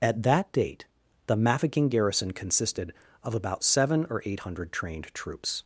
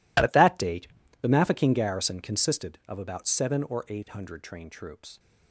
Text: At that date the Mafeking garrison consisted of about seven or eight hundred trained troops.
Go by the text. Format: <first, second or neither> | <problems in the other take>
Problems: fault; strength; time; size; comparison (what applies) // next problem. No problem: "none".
first | gets quieter; strong; throughout; 15.5 dB // pauses between "date" and "the"; slight; at 0.8 s; 0.32 s long; also in the first